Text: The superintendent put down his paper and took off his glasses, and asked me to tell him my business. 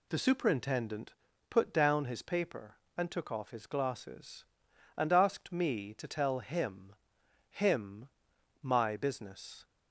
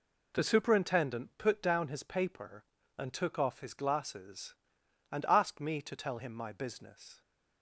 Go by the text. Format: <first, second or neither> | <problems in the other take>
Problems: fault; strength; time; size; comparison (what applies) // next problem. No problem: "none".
second | pauses between "superintendent" and "put"; slight; at 1.1 s; 0.36 s long // says "him" twice; at 7.4 s